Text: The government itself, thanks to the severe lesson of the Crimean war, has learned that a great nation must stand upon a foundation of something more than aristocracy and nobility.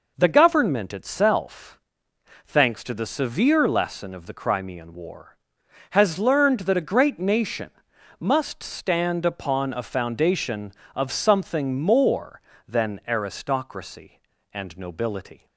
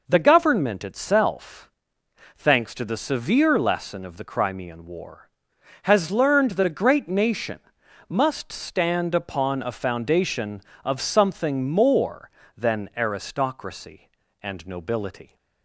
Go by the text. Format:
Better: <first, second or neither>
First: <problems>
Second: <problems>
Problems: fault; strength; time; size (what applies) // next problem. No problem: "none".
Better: neither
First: pauses between "nation" and "must"; noticeable; at 7.7 s; 0.50 s long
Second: pauses between "nation" and "must"; noticeable; at 7.5 s; 0.50 s long